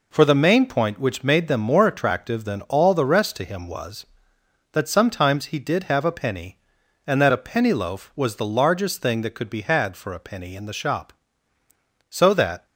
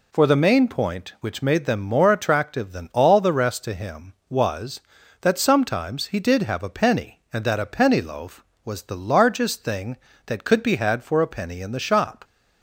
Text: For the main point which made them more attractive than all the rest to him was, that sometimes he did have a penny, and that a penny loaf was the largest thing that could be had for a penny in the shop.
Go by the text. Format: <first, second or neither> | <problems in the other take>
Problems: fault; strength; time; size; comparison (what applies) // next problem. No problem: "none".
second | goes on to say "So that"; from 12.0 s on; 0.56 s long